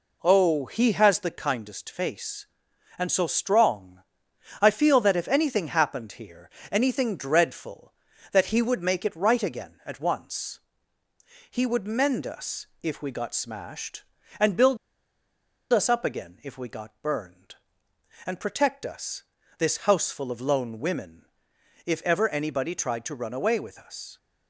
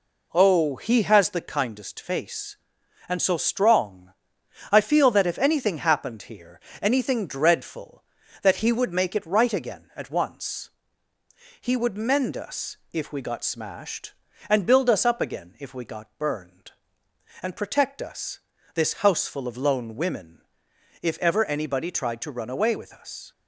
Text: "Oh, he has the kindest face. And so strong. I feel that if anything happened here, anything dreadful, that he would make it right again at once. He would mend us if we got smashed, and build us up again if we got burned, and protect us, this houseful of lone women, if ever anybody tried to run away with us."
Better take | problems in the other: second | pauses between "us" and "if"; slight; at 12.6 s; 0.16 s long; slight in the second // pauses between "build" and "us"; noticeable; at 14.7 s; 0.95 s long

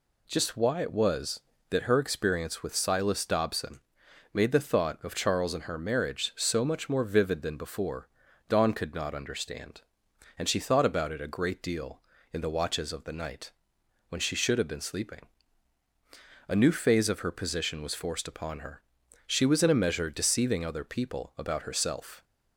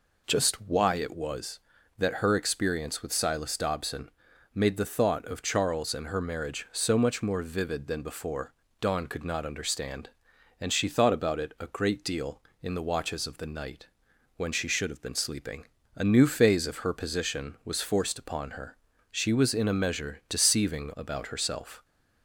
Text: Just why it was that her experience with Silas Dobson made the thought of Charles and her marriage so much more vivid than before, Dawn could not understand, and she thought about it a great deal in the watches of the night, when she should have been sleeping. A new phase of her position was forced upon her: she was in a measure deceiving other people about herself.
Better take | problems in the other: first | pauses between "Dobson" and "made"; at 4.0 s; 0.44 s long; noticeable in the first // skips "other people"; at 20.9 s

